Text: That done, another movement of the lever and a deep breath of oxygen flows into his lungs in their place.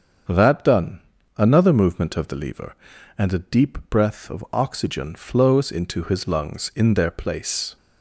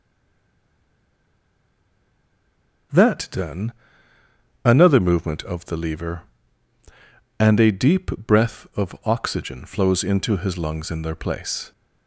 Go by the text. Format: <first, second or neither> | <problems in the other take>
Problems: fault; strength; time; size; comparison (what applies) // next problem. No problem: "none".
first | stays silent before the first word; strong; until 2.9 s; 2.9 s long // starts louder than the rest; until 4.8 s; 6.5 dB; also in the first